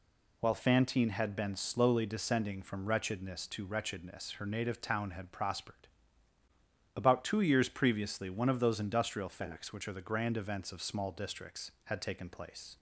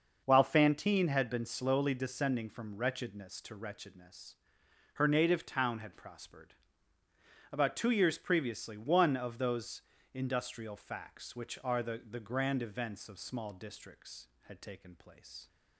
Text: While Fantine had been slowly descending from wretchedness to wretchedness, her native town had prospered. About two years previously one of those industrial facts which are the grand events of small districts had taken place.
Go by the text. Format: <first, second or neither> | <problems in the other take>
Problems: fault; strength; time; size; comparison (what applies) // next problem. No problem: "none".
first | starts louder than the rest; until 1.2 s; 6 dB // pauses between "those" and "industrial"; slight; at 9.8 s; 0.32 s long // says "the" twice; at 12.0 s